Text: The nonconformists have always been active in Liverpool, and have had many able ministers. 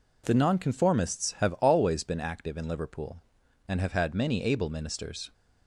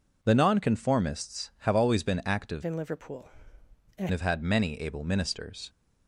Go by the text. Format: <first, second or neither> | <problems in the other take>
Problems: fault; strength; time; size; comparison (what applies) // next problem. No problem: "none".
first | changes voice from "in" to "and"; from 2.6 to 4.0 s; 1.4 s long